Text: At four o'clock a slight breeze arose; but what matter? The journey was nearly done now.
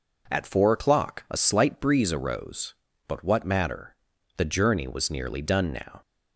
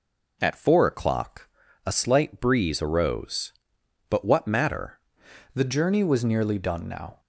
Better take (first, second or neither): first